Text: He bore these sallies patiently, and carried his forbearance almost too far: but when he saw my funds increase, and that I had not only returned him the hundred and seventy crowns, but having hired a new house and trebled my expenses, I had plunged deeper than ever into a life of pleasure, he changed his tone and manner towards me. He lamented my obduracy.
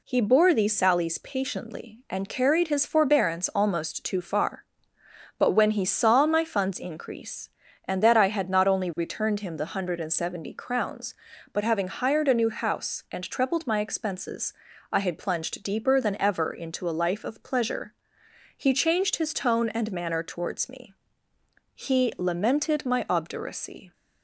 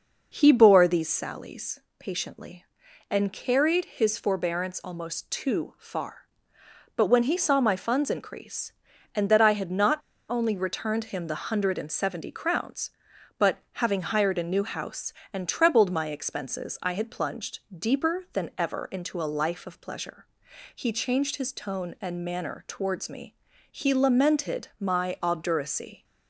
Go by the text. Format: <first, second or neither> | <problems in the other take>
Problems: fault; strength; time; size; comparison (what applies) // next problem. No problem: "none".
first | pauses between "sallies" and "patiently"; slight; at 1.7 s; 0.20 s long // pauses between "not" and "only"; slight; at 9.9 s; 0.30 s long // pauses between "but" and "having"; slight; at 13.5 s; 0.20 s long